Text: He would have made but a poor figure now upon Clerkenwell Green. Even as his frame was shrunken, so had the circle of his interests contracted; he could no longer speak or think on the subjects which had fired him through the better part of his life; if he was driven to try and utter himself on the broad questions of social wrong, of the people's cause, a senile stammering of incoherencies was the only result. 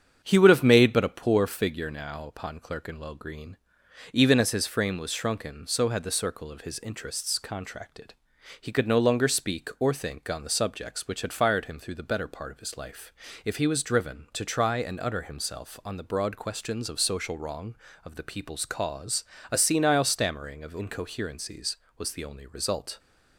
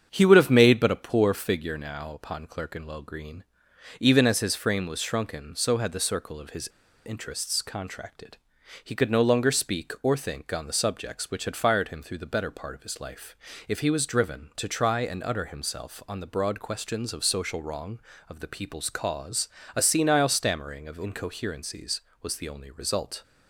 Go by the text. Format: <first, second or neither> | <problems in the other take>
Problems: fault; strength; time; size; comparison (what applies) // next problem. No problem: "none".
first | starts louder than the rest; strong; until 1.1 s; 8 dB; strong in the first // pauses between "his" and "interests"; at 6.6 s; 0.39 s long